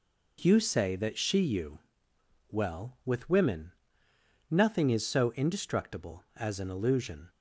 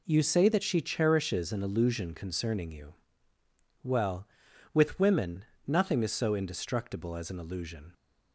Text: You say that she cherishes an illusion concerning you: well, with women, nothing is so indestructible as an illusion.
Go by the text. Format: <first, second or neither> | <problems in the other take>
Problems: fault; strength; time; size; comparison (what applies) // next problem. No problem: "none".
second | skips "cherishes an illusion concerning"; at 1.4 s